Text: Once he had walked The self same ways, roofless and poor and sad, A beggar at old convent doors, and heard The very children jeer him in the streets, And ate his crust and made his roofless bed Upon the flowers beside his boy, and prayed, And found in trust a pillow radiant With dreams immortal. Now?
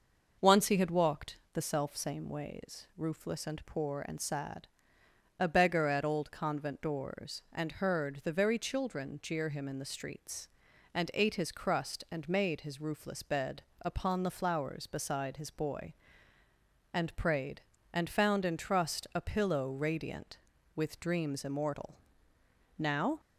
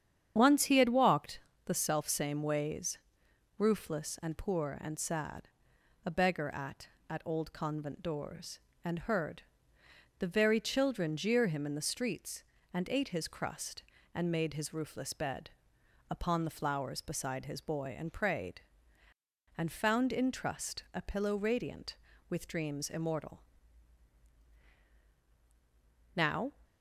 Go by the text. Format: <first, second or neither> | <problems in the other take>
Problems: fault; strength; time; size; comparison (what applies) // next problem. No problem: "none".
first | starts louder than the rest; strong; until 1.3 s; 8.5 dB // pauses between "walked" and "The"; slight; at 1.3 s; 0.26 s long; slight in the first // says "at" twice; at 7.0 s // pauses between "heard" and "The"; noticeable; at 9.4 s; 0.78 s long // pauses between "bed" and "Upon"; noticeable; at 15.4 s; 0.62 s long; slight in the first